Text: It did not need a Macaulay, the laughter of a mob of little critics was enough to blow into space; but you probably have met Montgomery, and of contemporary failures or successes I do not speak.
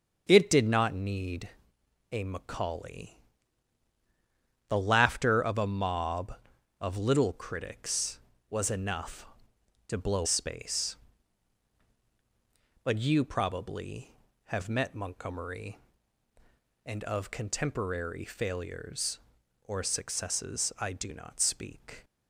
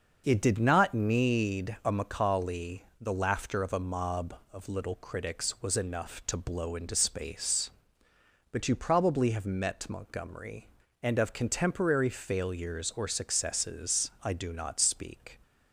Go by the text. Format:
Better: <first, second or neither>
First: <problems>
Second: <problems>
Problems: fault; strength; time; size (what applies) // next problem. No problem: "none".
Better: second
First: starts louder than the rest; until 1.2 s; 7 dB // pauses between "need" and "a"; noticeable; at 1.4 s; 0.64 s long // skips "into"; at 10.2 s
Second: starts louder than the rest; until 1.2 s; 6.5 dB